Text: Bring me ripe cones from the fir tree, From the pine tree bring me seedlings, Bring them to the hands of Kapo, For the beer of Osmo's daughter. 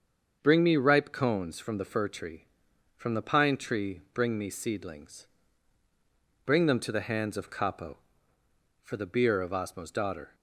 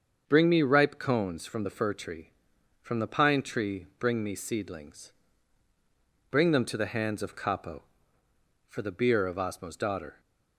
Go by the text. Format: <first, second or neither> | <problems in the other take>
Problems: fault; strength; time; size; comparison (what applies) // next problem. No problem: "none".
neither | starts louder than the rest; the same in both